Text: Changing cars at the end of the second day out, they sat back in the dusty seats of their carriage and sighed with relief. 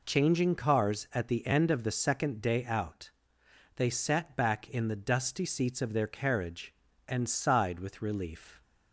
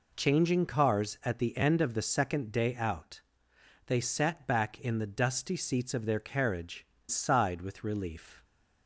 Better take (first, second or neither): first